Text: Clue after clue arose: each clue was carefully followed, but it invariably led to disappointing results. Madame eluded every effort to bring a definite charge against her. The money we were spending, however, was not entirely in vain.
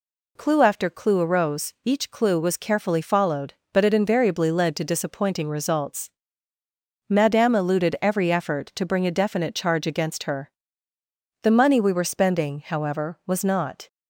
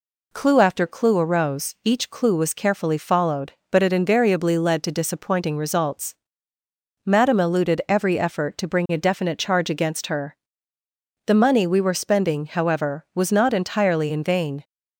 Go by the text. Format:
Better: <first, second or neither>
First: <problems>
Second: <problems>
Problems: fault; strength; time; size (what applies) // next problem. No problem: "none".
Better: second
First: stops before "entirely in vain"; at 13.8 s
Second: none